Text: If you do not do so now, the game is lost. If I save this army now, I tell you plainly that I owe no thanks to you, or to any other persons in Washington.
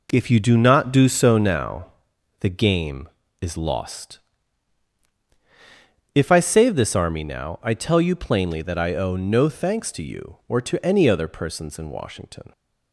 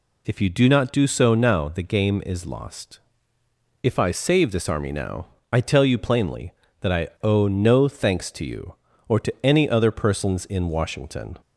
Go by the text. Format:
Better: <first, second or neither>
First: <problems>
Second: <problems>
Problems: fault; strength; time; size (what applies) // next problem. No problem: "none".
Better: neither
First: none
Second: none